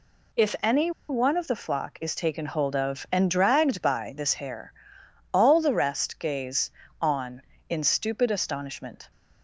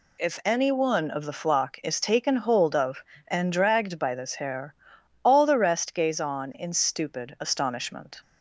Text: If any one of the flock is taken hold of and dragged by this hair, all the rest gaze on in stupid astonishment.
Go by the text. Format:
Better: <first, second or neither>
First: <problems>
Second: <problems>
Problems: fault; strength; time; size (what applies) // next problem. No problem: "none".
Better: second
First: pauses between "any" and "one"; slight; at 0.8 s; 0.19 s long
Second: none